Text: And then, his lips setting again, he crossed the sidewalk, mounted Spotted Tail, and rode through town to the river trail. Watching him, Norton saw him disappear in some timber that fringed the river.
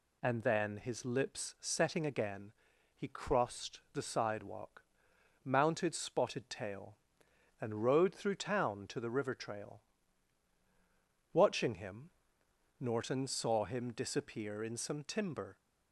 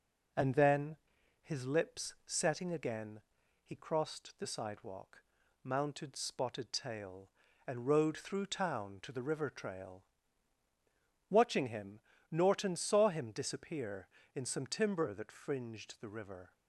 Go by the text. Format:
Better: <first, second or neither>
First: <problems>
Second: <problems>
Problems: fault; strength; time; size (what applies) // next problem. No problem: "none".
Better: second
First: stops before "that fringed the river"; at 15.5 s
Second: none